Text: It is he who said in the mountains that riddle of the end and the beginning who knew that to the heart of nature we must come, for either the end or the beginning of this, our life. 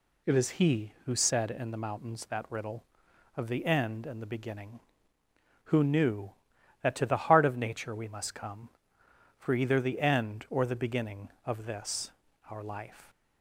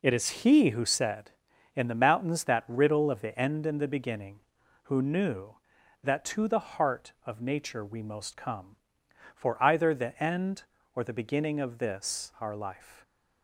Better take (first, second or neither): first